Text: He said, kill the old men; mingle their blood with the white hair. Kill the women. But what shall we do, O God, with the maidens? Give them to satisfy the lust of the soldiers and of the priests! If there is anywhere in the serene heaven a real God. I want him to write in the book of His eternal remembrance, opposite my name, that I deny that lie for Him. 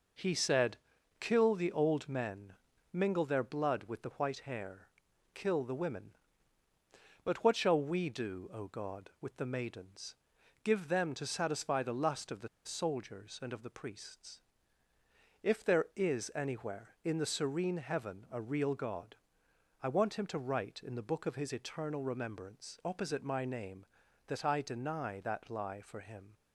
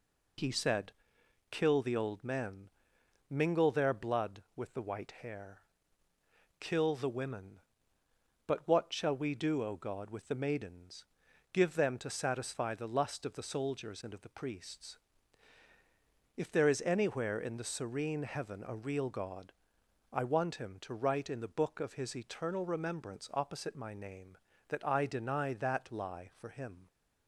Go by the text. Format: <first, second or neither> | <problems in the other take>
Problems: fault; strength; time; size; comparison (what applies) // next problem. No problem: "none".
second | pauses between "the" and "soldiers"; slight; at 12.4 s; 0.18 s long